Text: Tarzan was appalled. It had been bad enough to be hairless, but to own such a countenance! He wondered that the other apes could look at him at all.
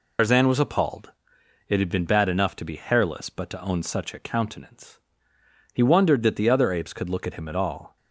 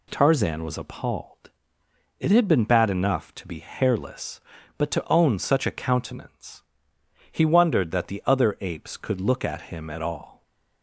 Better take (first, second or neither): second